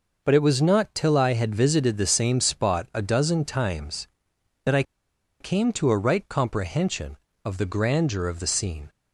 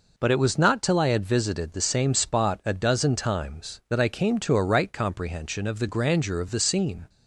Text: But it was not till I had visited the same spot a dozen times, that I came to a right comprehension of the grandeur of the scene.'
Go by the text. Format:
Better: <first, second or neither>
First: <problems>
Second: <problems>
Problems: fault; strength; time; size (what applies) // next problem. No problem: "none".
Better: second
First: pauses between "I" and "came"; noticeable; at 4.8 s; 0.57 s long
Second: none